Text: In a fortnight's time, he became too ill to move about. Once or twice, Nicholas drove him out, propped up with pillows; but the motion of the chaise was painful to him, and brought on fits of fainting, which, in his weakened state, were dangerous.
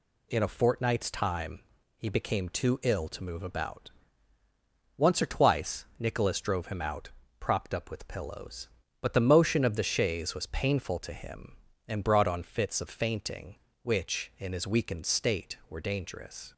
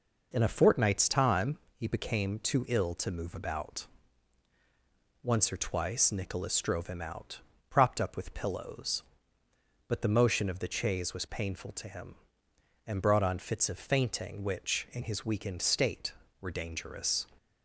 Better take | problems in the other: neither | none

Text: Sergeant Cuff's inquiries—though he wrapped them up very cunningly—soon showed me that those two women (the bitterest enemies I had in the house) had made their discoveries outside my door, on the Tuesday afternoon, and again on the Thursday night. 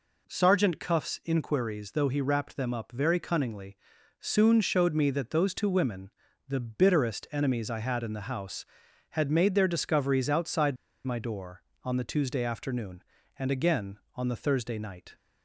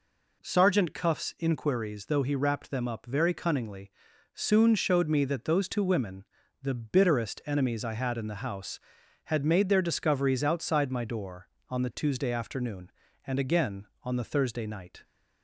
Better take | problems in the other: second | pauses between "outside" and "my"; slight; at 10.7 s; 0.31 s long

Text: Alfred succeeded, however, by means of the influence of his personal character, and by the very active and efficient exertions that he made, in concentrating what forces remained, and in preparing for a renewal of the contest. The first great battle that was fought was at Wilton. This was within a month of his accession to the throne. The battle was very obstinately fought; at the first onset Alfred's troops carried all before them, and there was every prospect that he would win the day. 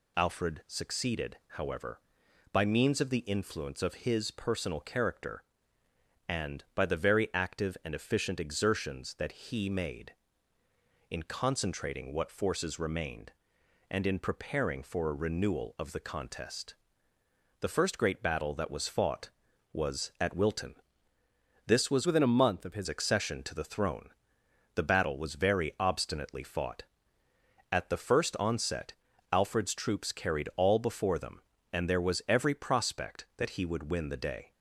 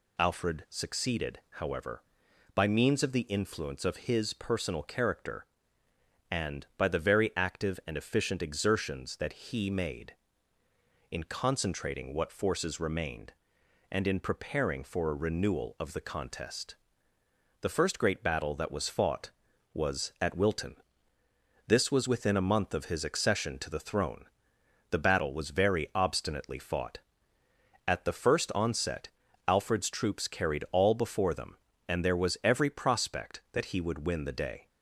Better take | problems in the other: second | changes voice from "within" to "his"; from 22.0 to 22.8 s; 0.8 s long // pauses between "onset" and "Alfred's"; at 28.9 s; 0.40 s long; also in the second

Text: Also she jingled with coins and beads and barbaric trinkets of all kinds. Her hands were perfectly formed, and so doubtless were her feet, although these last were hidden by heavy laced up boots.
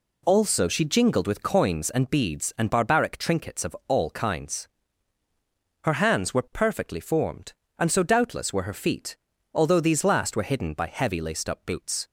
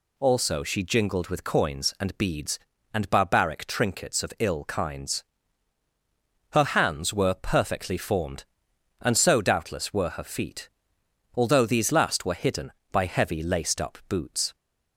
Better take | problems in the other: first | says "ill" for "all"; at 4.3 s

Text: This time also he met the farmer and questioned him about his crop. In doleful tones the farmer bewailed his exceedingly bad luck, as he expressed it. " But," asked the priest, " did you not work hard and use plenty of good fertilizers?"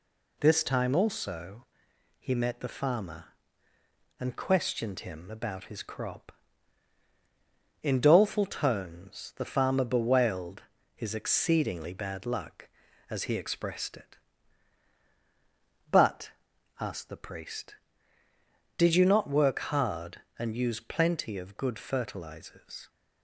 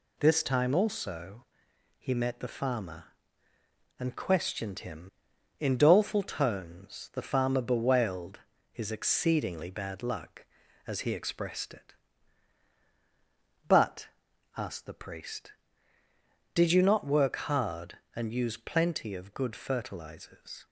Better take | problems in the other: first | pauses between "also" and "he"; noticeable; at 1.4 s; 0.56 s long; noticeable in the first // skips "about his crop"; at 5.3 s // pauses between "bewailed" and "his"; slight; at 8.3 s; 0.32 s long; slight in the first

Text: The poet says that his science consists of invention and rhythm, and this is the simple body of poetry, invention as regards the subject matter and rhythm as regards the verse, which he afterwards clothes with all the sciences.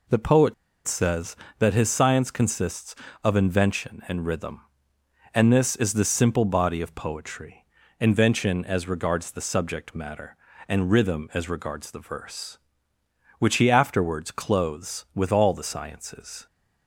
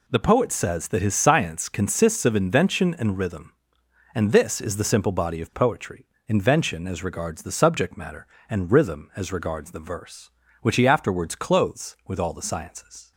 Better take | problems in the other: second | pauses between "poet" and "says"; slight; at 0.5 s; 0.31 s long

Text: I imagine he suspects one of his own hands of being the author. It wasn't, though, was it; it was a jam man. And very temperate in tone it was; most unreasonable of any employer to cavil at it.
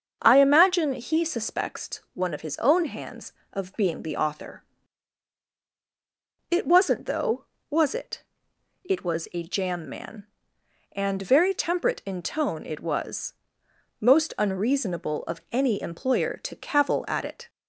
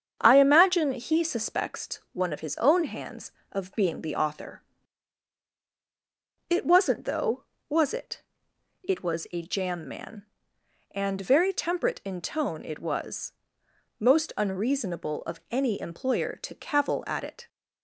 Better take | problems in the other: first | gets quieter; slight; throughout; 3 dB // starts louder than the rest; strong; until 1.2 s; 8 dB; also in the first

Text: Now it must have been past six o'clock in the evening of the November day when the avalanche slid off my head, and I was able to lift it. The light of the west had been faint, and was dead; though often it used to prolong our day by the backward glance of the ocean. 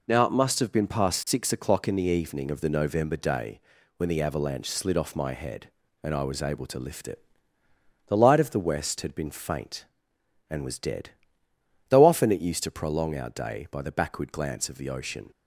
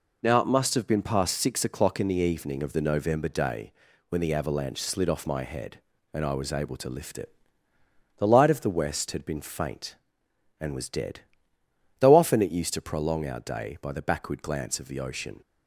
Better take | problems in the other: neither | pauses between "day" and "when"; slight; the same in both

